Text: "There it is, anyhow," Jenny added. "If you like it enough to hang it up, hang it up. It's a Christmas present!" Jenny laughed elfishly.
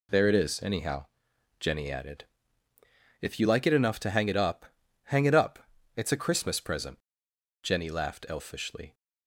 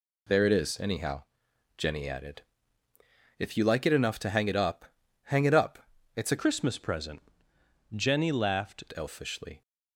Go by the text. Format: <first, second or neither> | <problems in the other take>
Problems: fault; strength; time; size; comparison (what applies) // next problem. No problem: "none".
first | changes voice from "Christmas" to "laughed"; from 6.3 to 8.8 s; 2.5 s long